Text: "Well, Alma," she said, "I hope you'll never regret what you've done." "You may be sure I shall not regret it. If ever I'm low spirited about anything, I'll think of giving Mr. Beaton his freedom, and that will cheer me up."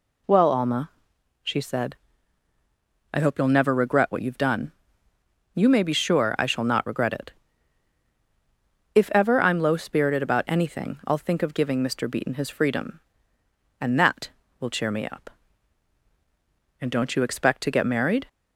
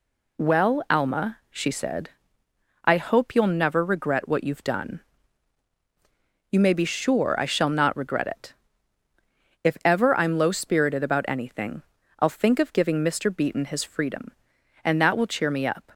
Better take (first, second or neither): second